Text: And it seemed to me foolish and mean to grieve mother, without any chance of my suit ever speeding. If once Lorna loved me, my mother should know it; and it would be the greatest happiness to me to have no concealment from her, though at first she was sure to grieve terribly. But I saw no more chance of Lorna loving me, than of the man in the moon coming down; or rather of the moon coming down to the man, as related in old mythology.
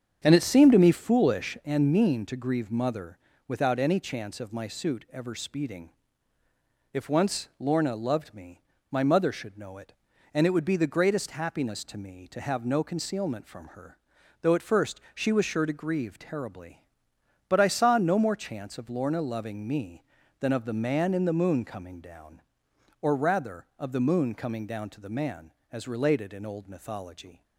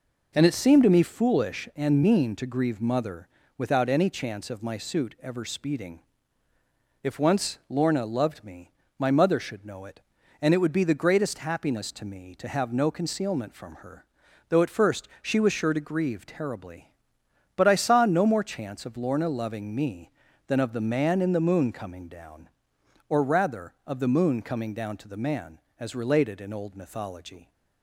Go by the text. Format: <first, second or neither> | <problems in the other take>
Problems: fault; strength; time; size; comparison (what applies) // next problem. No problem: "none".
second | starts louder than the rest; strong; until 1.9 s; 7.5 dB